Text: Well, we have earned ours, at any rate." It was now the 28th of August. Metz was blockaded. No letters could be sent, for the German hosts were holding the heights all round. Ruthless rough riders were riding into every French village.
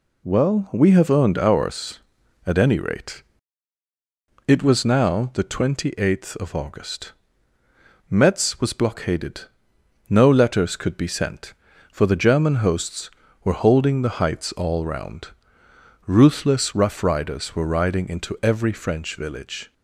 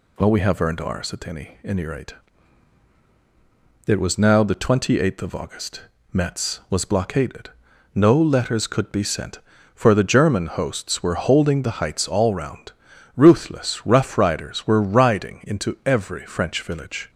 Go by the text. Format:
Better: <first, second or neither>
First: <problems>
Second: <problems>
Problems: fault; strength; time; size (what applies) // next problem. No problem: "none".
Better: first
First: none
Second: says "any" twice; at 1.6 s